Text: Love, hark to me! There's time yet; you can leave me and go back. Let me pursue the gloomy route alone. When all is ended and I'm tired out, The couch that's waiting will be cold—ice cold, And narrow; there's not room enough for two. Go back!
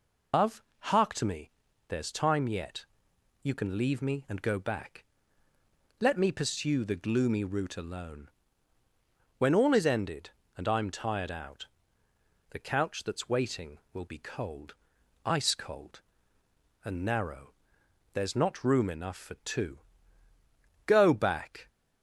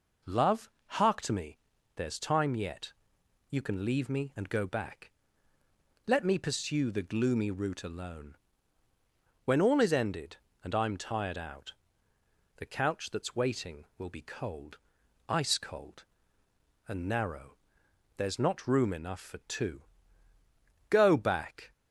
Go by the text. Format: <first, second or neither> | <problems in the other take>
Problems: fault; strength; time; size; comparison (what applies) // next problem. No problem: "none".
second | loses the start of "Love"; at 0.3 s; 165 ms